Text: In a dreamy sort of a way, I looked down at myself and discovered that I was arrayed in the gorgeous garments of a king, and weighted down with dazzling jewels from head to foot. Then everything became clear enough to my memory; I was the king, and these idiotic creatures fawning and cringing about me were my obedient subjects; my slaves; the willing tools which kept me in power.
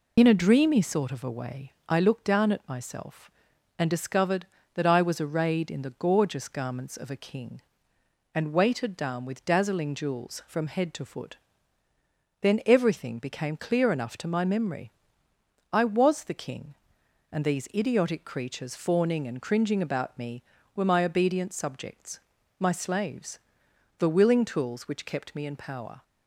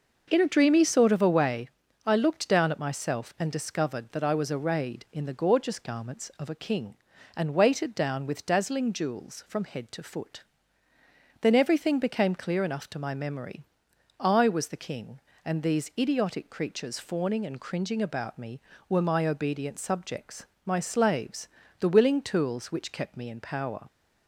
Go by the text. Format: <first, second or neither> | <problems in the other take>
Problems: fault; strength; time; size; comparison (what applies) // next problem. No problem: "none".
second | loses the start of "In"; at 0.1 s; 50 ms